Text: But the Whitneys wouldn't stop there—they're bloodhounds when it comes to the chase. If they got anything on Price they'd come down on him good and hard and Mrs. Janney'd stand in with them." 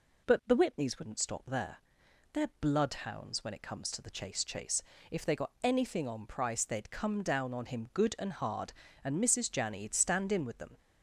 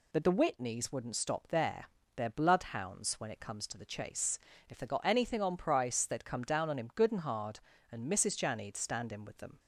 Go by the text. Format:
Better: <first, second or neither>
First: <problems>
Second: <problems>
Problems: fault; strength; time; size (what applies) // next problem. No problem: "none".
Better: second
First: says "chase" twice; at 4.4 s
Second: none